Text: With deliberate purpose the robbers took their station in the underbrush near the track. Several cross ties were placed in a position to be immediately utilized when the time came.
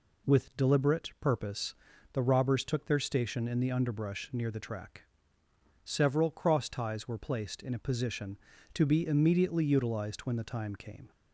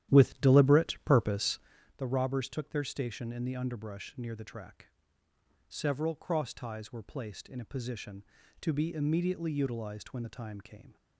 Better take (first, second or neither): first